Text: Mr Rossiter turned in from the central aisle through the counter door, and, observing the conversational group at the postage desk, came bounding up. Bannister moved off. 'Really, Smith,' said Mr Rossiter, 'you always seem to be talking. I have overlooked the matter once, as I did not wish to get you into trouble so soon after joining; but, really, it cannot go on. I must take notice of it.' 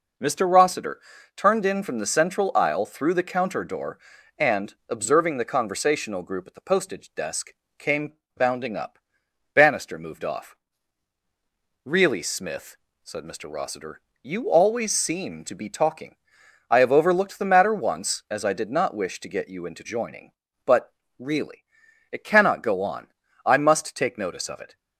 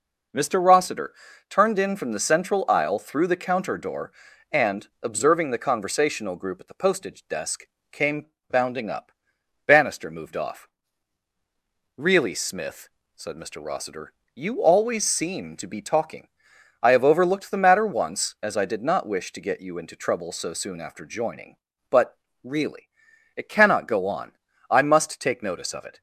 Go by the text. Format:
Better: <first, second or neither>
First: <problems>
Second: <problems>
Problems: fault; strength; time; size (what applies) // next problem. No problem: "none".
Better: second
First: pauses between "Rossiter" and "turned"; slight; at 1.0 s; 0.36 s long // pauses between "came" and "bounding"; slight; at 8.1 s; 0.22 s long // skips "trouble so soon after"; at 19.8 s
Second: pauses between "Rossiter" and "turned"; slight; at 1.1 s; 0.36 s long // pauses between "came" and "bounding"; slight; at 8.2 s; 0.22 s long